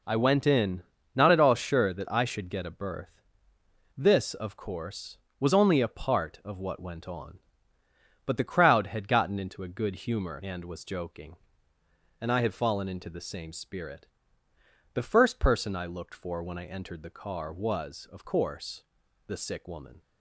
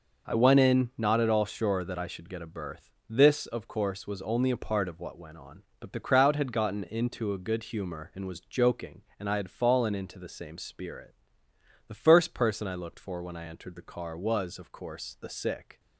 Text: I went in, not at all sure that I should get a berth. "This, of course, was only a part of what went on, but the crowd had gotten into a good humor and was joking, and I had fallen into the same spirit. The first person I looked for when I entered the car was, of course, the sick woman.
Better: first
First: none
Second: stops before "woman"; at 15.7 s

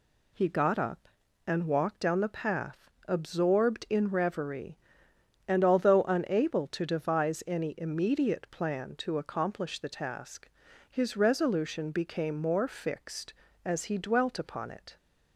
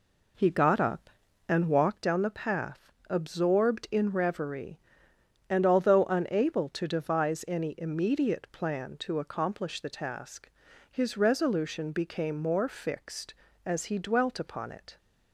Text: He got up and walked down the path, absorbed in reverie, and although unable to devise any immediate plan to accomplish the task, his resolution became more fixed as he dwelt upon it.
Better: first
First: none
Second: starts louder than the rest; slight; until 2.0 s; 3 dB

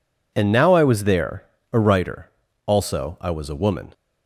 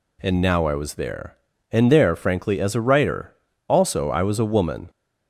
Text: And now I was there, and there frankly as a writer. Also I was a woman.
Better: second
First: skips "and there frankly as"; at 1.5 s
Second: none

